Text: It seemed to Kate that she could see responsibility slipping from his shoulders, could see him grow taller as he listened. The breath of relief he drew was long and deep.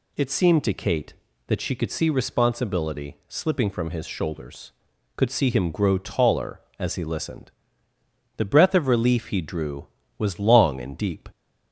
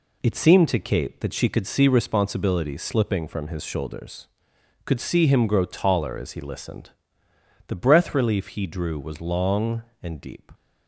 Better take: first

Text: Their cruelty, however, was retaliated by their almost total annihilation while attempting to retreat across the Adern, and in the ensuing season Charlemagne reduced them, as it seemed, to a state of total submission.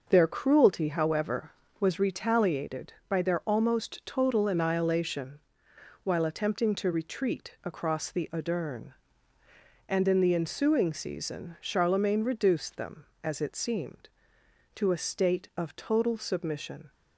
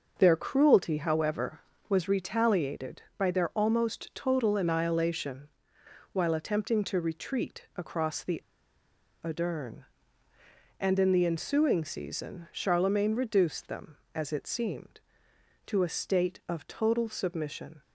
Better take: first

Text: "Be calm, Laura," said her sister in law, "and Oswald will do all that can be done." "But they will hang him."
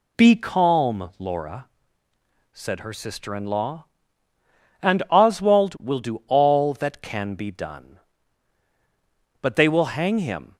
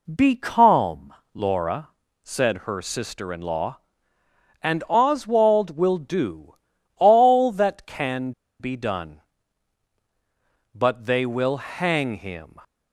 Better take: first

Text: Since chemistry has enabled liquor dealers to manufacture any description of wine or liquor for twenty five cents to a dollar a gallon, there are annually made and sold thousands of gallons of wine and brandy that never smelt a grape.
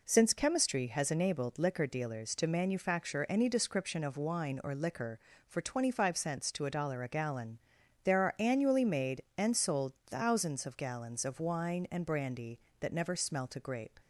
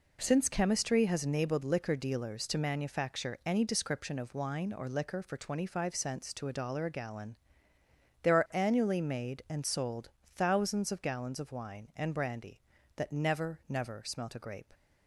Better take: first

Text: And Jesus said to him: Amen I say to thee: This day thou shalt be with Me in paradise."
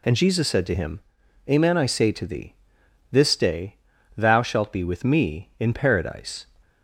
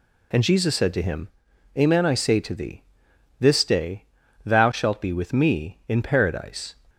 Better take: neither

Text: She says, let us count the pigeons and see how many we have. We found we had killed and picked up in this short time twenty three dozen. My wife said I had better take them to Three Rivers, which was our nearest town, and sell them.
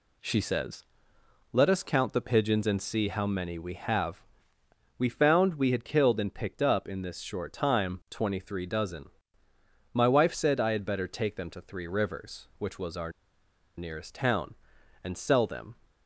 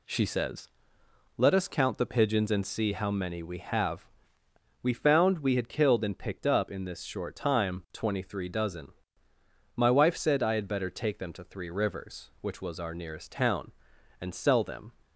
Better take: second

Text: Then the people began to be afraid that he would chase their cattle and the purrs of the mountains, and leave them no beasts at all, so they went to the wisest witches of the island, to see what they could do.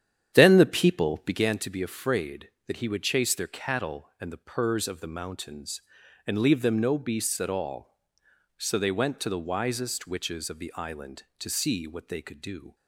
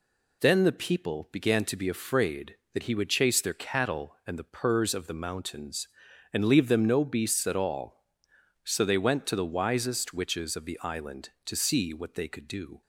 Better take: second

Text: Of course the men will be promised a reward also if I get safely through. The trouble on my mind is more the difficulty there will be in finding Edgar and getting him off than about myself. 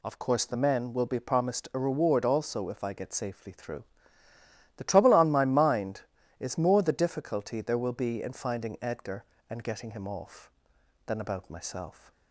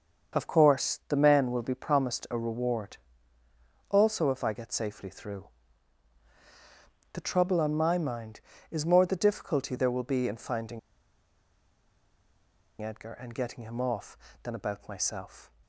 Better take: first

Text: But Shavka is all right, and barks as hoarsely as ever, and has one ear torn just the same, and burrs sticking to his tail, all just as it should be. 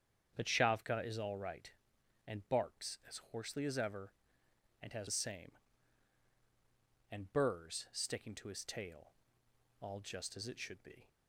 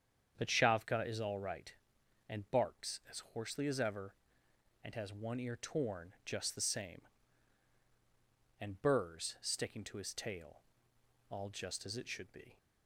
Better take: second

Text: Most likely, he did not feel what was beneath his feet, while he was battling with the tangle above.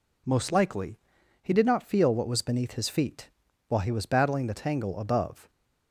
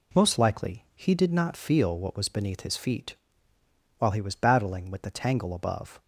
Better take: second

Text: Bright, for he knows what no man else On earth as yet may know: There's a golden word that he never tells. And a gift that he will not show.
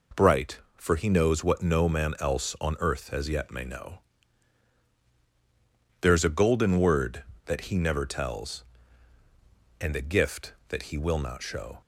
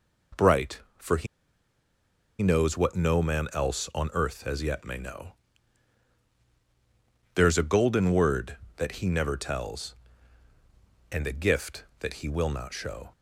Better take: first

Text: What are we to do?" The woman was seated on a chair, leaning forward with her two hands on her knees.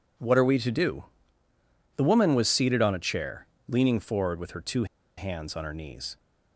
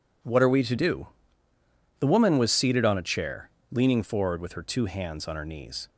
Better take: second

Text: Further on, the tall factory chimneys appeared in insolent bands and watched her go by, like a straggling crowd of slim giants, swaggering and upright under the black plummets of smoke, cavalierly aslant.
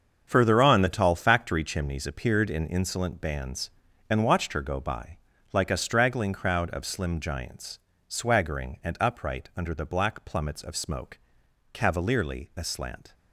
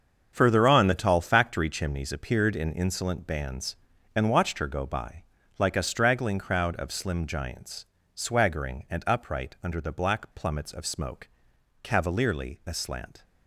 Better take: neither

